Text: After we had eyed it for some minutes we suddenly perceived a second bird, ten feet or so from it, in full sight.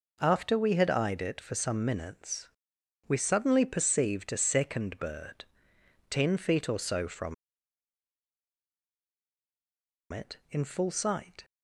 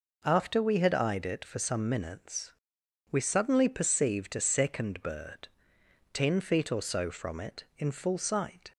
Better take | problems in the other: second | pauses between "minutes" and "we"; noticeable; at 2.4 s; 0.58 s long; noticeable in the second // pauses between "from" and "it"; strong; at 7.3 s; 2.7 s long

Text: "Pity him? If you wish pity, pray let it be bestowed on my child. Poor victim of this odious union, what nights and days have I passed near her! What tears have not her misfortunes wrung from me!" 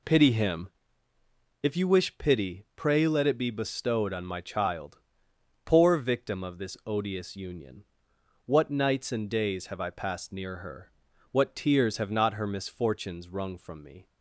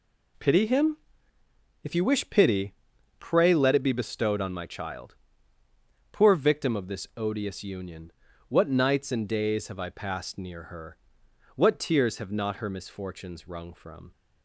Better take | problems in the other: first | stops before "me"; at 14.1 s

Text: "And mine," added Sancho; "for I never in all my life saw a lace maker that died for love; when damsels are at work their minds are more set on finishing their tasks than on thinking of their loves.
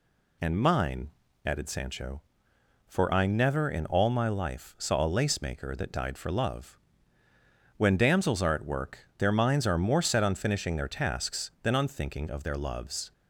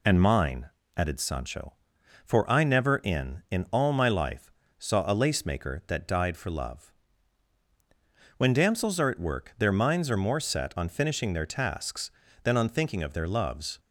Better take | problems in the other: first | says "in" twice; at 3.5 s // pauses between "life" and "saw"; slight; at 4.5 s; 0.26 s long

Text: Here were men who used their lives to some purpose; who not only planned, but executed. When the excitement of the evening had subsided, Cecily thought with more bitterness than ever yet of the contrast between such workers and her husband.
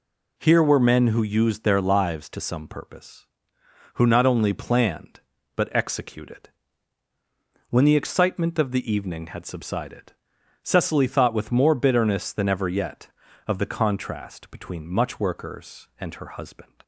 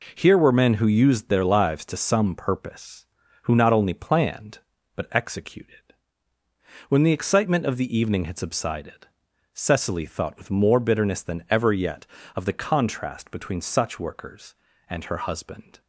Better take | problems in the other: second | says "much" for "such"; at 14.8 s

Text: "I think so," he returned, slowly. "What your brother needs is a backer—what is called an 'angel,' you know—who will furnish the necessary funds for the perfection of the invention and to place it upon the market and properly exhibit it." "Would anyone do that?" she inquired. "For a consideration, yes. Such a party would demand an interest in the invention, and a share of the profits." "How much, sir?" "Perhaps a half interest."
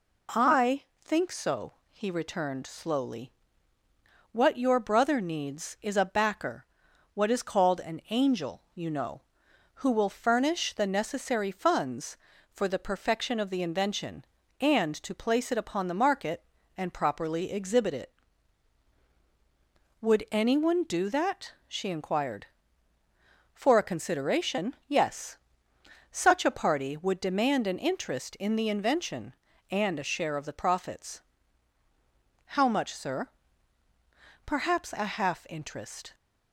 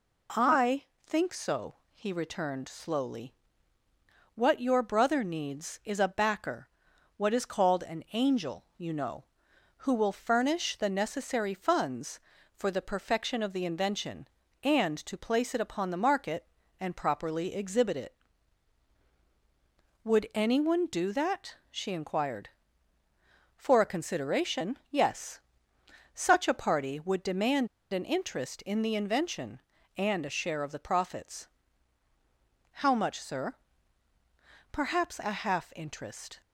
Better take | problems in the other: first | pauses between "I" and "think"; slight; at 0.8 s; 0.18 s long; slight in the first // pauses between "demand" and "an"; slight; at 27.6 s; 0.24 s long

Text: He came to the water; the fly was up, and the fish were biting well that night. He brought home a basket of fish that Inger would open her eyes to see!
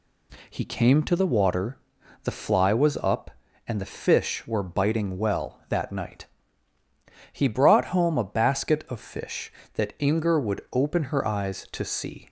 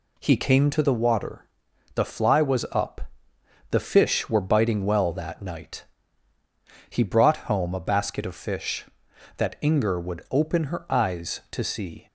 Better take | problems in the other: first | skips "and"; at 3.3 s

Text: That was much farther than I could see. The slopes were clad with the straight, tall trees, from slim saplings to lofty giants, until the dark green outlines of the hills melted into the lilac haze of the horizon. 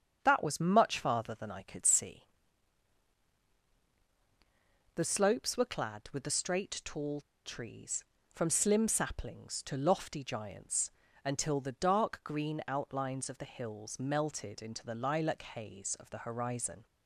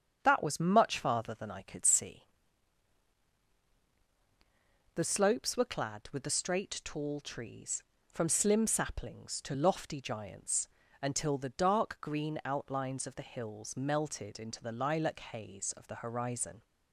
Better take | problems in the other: second | starts louder than the rest; strong; until 1.2 s; 7.5 dB; strong in the second // pauses between "tall" and "trees"; slight; at 7.2 s; 0.23 s long

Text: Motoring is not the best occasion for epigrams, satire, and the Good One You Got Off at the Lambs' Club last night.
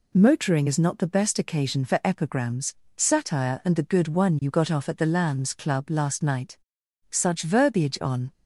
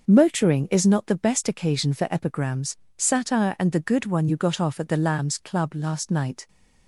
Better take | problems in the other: second | goes on to say "Such verbiage on"; noticeable; from 7.0 s on; 1.2 s long

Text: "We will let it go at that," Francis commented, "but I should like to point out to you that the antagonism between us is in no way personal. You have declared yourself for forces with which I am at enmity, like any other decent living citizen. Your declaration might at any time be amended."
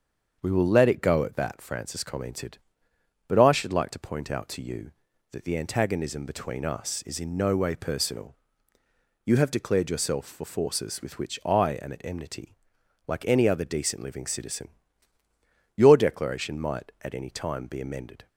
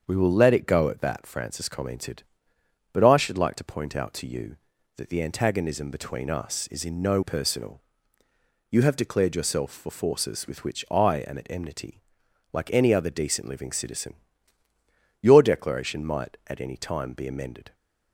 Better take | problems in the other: first | starts louder than the rest; strong; until 1.0 s; 7 dB; also in the first // skips "way"; at 7.2 s

